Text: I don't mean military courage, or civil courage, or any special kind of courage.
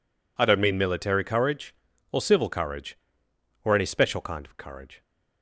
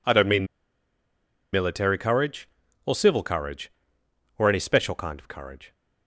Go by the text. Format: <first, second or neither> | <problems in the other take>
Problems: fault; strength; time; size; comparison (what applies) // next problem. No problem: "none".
first | pauses between "mean" and "military"; at 0.4 s; 1.0 s long